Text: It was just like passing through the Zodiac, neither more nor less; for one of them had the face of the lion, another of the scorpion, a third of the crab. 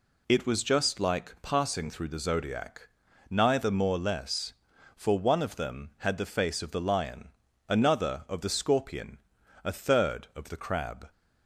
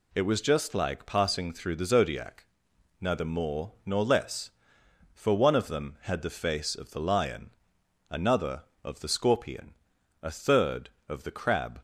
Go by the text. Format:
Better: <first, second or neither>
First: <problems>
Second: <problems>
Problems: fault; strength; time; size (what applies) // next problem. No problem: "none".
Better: second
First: skips "nor"; at 3.9 s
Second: none